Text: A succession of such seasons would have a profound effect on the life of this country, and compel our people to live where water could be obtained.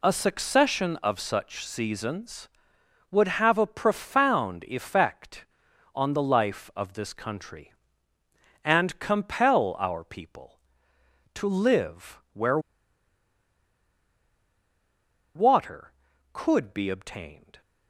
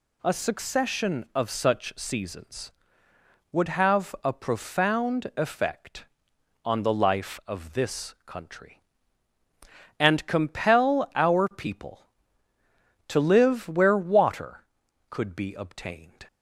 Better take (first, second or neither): second